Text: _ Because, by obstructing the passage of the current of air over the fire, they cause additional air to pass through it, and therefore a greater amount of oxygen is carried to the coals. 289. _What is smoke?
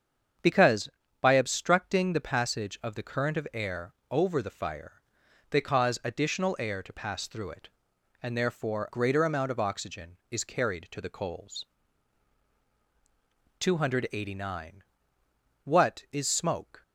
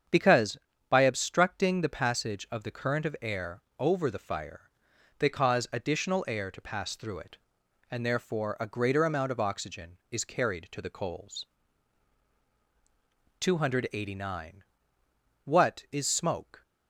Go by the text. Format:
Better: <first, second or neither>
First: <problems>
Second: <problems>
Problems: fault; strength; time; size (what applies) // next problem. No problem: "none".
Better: second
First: starts louder than the rest; strong; until 1.7 s; 7.5 dB // pauses between "air" and "over"; slight; at 3.9 s; 0.18 s long // skips "a"; at 8.8 s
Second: starts louder than the rest; strong; until 1.4 s; 7.5 dB // pauses between "air" and "over"; slight; at 3.6 s; 0.18 s long